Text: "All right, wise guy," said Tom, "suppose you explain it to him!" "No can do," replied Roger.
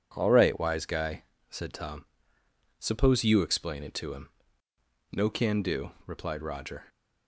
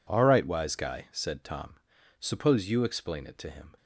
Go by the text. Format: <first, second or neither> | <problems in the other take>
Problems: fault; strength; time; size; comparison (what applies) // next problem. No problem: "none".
first | stops before "No can do replied Roger"; at 3.7 s